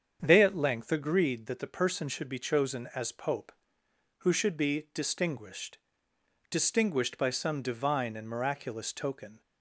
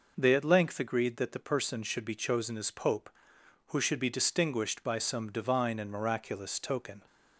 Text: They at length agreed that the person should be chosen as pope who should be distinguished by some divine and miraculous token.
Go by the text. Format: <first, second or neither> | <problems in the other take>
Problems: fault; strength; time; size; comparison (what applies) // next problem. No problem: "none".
second | starts louder than the rest; strong; until 1.2 s; 7.5 dB // says "distinguished" twice; at 6.5 s